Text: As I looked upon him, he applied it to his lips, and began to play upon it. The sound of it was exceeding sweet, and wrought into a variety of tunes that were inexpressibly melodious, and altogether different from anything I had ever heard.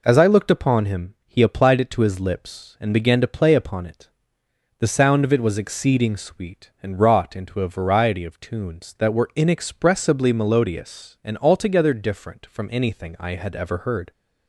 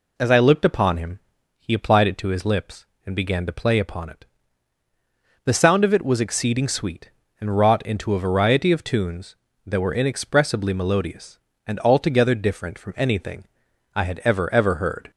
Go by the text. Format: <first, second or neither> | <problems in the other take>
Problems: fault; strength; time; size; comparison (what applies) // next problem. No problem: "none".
first | pauses between "anything" and "I"; noticeable; at 13.4 s; 0.50 s long // says "ever" twice; at 14.5 s